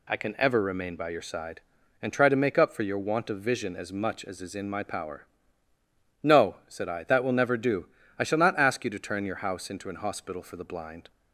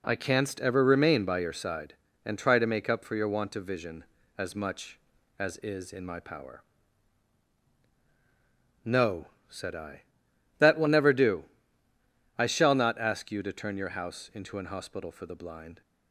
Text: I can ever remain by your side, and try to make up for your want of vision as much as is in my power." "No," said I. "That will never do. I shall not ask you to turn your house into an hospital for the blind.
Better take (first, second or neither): first